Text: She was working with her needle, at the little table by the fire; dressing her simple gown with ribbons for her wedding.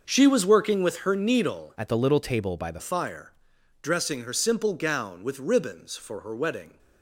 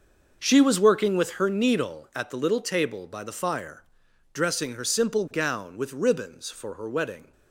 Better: second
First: starts louder than the rest; noticeable; until 1.0 s; 6 dB // changes voice from "at" to "the"; from 1.7 to 2.7 s; 1.0 s long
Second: starts louder than the rest; noticeable; until 1.4 s; 6 dB

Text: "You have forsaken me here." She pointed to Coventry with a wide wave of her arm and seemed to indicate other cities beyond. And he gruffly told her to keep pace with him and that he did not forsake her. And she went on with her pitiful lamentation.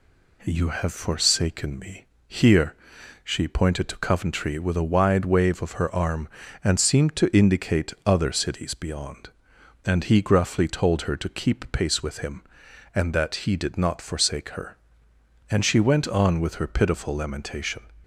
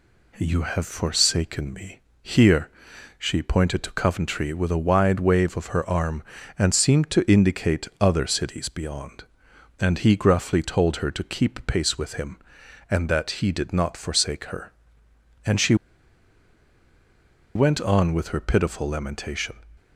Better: first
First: pauses between "me" and "here"; slight; at 2.0 s; 0.24 s long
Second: pauses between "me" and "here"; slight; at 1.9 s; 0.24 s long // pauses between "she" and "went"; strong; at 15.7 s; 1.8 s long

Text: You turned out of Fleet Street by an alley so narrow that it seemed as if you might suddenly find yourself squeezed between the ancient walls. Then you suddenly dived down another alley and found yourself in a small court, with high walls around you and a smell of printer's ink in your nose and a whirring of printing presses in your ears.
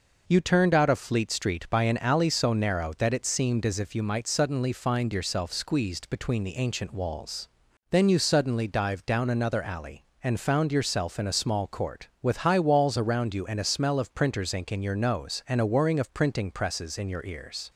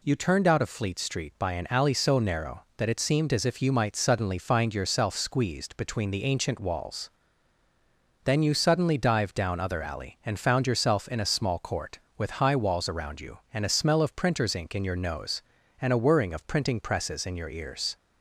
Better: first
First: none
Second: says "other" for "another"; at 9.6 s

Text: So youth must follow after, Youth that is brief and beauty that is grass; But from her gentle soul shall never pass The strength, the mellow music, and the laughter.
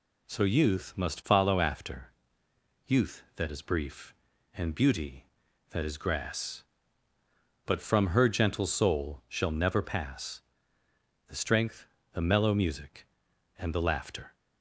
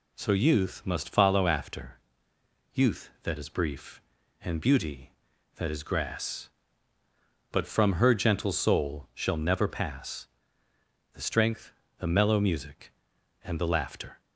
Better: neither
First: pauses between "pass" and "The"; noticeable; at 10.4 s; 0.88 s long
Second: pauses between "pass" and "The"; noticeable; at 10.2 s; 0.88 s long

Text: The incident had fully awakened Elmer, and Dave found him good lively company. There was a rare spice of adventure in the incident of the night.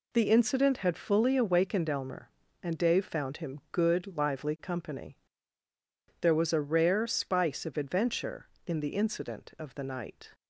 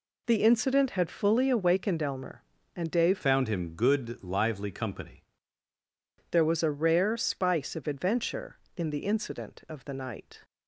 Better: first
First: none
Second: changes voice from "found" to "company"; from 3.2 to 5.2 s; 2.0 s long

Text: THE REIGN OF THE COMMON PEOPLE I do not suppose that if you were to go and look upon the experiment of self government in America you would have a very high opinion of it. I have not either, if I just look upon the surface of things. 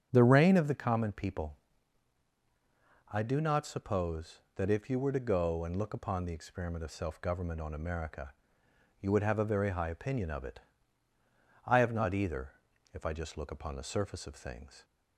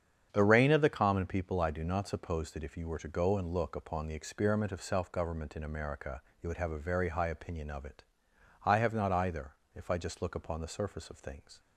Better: second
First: starts louder than the rest; strong; until 1.1 s; 8.5 dB // pauses between "PEOPLE" and "I"; strong; at 1.5 s; 1.5 s long // says "on" for "in"; at 7.6 s // pauses between "America" and "you"; noticeable; at 8.3 s; 0.68 s long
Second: starts louder than the rest; strong; until 1.3 s; 8 dB // pauses between "America" and "you"; slight; at 6.2 s; 0.18 s long

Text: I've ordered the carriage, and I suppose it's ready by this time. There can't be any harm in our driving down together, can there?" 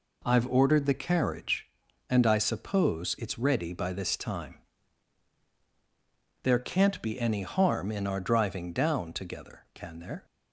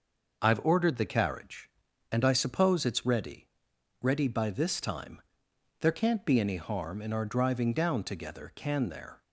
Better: first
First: none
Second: says "ready" twice; at 4.0 s

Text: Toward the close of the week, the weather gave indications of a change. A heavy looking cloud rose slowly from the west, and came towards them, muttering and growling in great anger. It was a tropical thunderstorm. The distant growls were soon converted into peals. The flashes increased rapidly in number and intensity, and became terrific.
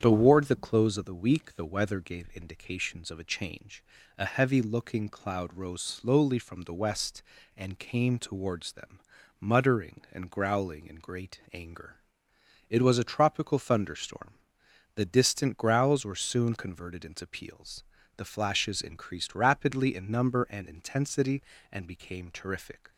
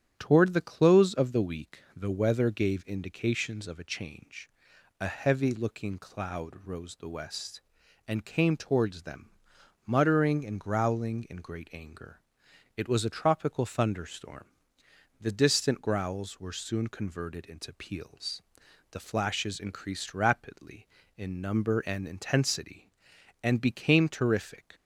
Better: first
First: starts louder than the rest; strong; until 1.0 s; 8.5 dB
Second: starts louder than the rest; strong; until 1.1 s; 9.5 dB // skips "slowly from"; at 6.9 s

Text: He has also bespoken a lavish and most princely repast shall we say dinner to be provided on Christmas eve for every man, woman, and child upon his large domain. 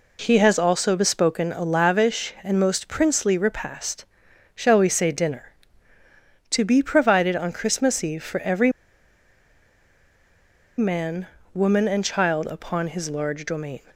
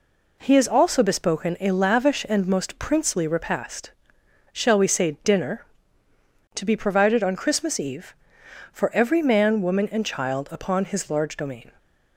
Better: second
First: pauses between "repast" and "shall"; noticeable; at 4.0 s; 0.50 s long // pauses between "every" and "man"; strong; at 8.6 s; 2.0 s long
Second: pauses between "repast" and "shall"; noticeable; at 3.9 s; 0.60 s long

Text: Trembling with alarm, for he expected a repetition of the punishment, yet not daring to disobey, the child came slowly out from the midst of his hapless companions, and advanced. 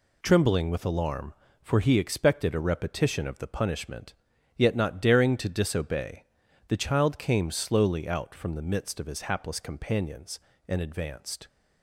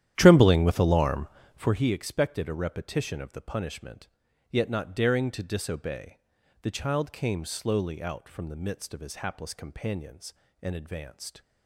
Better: first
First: none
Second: starts louder than the rest; strong; until 1.7 s; 11 dB

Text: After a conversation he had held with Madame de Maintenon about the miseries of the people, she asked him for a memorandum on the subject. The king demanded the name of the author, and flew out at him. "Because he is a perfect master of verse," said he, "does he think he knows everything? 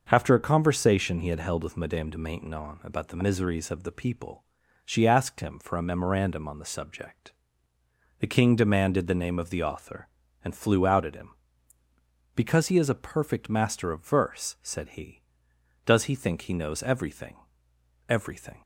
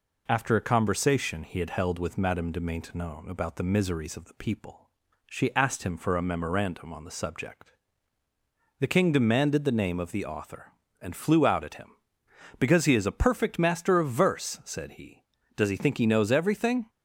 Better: second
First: starts louder than the rest; until 1.1 s; 6.5 dB // says "everything" twice; at 18.0 s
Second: none

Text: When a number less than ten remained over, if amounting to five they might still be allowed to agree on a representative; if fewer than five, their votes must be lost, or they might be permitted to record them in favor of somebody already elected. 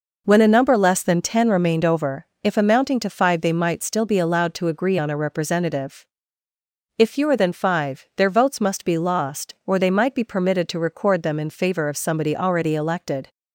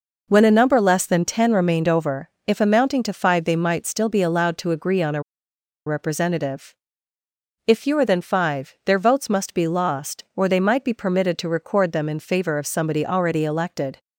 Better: first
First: none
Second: pauses between "a" and "representative"; noticeable; at 5.2 s; 0.64 s long

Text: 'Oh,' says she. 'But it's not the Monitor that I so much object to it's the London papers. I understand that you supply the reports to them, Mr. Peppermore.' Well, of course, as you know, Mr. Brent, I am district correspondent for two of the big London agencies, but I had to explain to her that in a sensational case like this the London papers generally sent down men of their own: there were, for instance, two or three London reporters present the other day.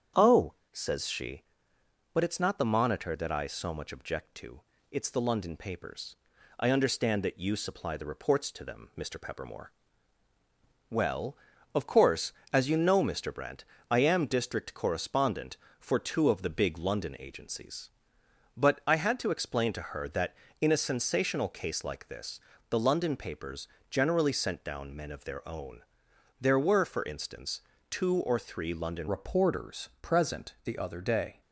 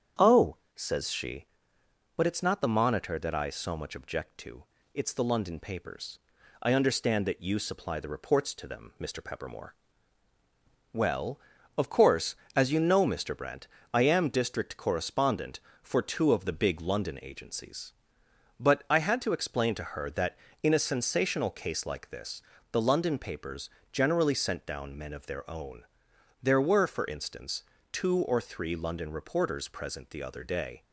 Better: second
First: starts louder than the rest; strong; until 1.3 s; 8 dB // pauses between "to" and "it's"; slight; at 4.6 s; 0.30 s long // pauses between "this" and "the"; slight; at 22.3 s; 0.30 s long // pauses between "papers" and "generally"; slight; at 23.6 s; 0.24 s long // changes voice at "reporters"; from 29.0 s on; 2.4 s long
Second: starts louder than the rest; strong; until 1.3 s; 8 dB // pauses between "to" and "it's"; slight; at 4.6 s; 0.30 s long // pauses between "this" and "the"; slight; at 22.4 s; 0.30 s long // pauses between "papers" and "generally"; slight; at 23.6 s; 0.24 s long

